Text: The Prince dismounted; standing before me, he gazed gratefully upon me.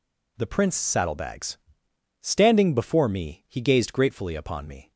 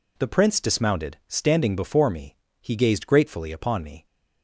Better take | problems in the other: second | says "saddlebags" for "dismounted"; at 0.7 s

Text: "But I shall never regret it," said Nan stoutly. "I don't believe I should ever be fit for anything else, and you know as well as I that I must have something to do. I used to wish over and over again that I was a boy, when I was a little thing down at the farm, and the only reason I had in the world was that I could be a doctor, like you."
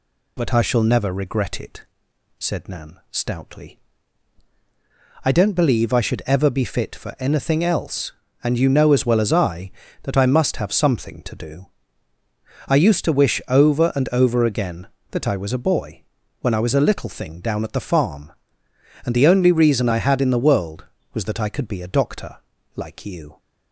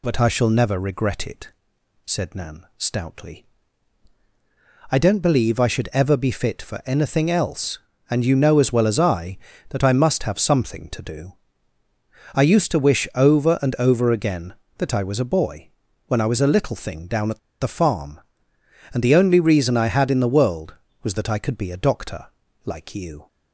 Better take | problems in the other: first | pauses between "at" and "the"; slight; at 17.3 s; 0.22 s long

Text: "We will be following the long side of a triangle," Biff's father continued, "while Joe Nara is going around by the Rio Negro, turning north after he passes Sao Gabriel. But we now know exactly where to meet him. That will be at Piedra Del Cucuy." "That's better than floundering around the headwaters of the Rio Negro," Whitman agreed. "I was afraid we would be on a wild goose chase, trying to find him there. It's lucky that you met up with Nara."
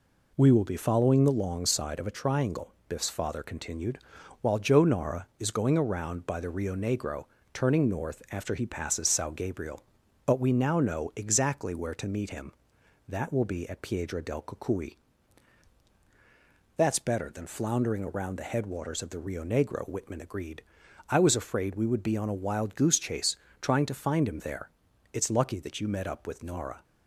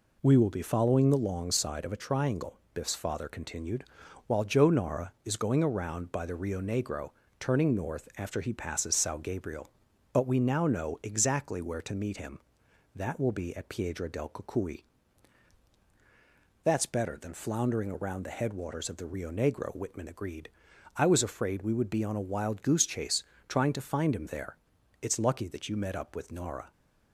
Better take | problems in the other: neither | none

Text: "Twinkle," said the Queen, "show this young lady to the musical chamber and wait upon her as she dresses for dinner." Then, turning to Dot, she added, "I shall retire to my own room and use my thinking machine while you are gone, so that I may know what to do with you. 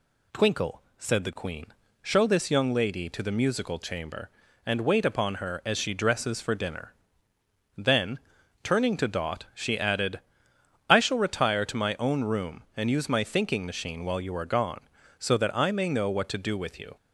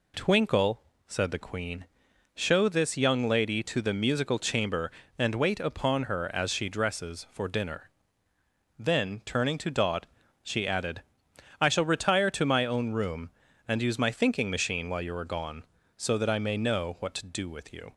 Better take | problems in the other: neither | none

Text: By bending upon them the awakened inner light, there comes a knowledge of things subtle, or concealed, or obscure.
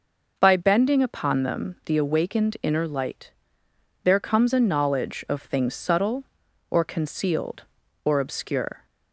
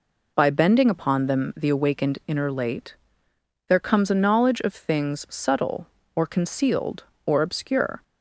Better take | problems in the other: first | says "late" for "light"; at 2.5 s

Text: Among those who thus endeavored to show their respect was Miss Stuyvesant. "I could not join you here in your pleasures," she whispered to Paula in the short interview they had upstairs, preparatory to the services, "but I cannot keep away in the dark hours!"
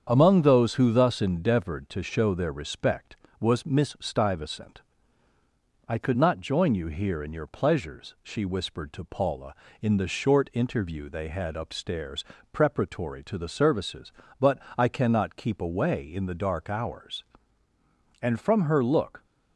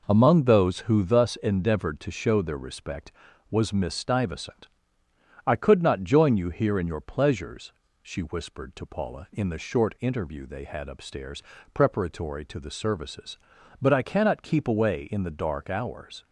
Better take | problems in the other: second | starts louder than the rest; strong; until 1.1 s; 7.5 dB // pauses between "but" and "I"; slight; at 14.6 s; 0.18 s long // goes on to say "And from her look"; noticeable; from 18.2 s on; 1.0 s long

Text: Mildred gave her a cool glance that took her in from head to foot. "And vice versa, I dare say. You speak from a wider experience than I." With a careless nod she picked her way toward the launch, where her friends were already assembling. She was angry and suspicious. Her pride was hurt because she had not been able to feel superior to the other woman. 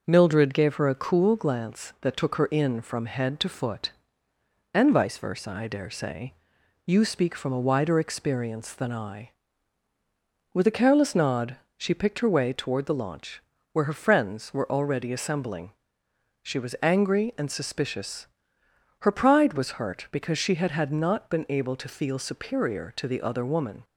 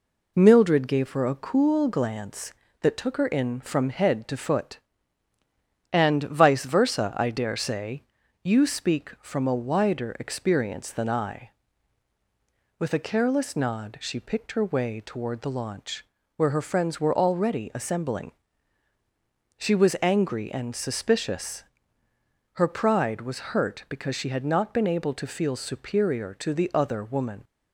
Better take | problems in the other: second | pauses between "nod" and "she"; slight; at 11.5 s; 0.22 s long // says "had" twice; at 20.7 s

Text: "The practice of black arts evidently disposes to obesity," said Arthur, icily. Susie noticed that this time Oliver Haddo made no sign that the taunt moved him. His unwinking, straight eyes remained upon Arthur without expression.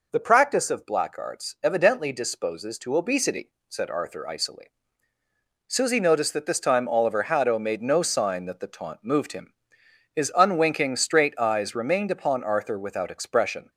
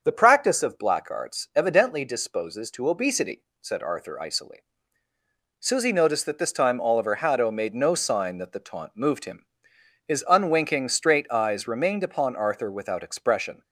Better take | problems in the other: first | starts louder than the rest; until 1.9 s; 6.5 dB

